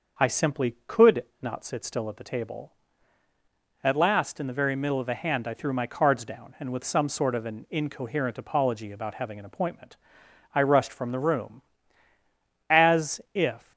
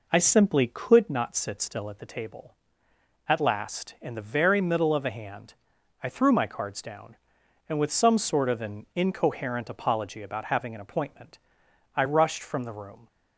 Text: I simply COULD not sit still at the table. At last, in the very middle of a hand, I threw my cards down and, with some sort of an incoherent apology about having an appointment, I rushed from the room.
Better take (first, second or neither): second